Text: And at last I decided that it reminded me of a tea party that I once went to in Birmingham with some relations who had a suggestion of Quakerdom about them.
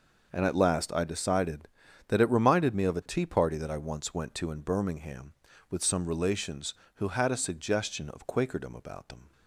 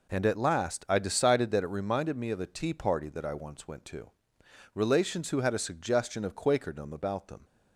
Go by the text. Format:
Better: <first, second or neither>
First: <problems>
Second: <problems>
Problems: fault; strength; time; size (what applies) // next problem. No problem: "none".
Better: first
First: none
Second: skips "in Birmingham with some"; at 4.4 s